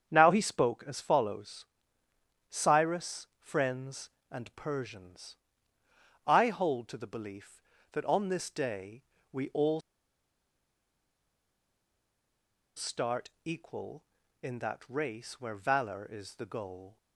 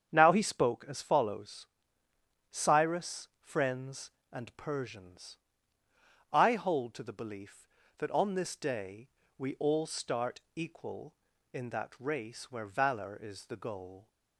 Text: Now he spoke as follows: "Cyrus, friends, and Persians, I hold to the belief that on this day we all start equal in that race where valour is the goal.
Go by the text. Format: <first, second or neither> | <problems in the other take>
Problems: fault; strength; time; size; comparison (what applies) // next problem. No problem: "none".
second | starts louder than the rest; strong; until 1.1 s; 8 dB; strong in the second // pauses between "day" and "we"; slight; at 9.0 s; 0.30 s long; slight in the second // pauses between "all" and "start"; strong; at 9.8 s; 2.9 s long // pauses between "start" and "equal"; slight; at 13.2 s; 0.16 s long; slight in the second